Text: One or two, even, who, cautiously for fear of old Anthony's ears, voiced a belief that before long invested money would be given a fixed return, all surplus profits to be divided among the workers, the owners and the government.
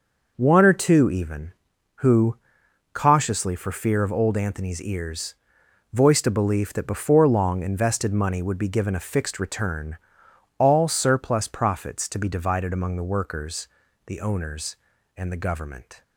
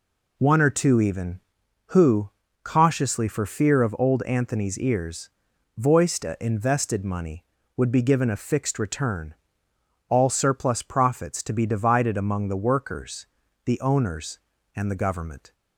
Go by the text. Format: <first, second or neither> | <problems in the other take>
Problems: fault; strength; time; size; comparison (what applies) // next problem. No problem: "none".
first | skips "belief that before long"; at 6.3 s